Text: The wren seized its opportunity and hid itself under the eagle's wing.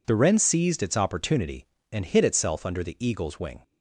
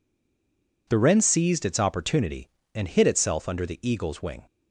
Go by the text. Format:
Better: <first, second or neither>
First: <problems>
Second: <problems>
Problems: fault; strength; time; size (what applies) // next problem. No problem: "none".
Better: first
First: none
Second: stays silent before the first word; slight; until 0.8 s; 0.8 s long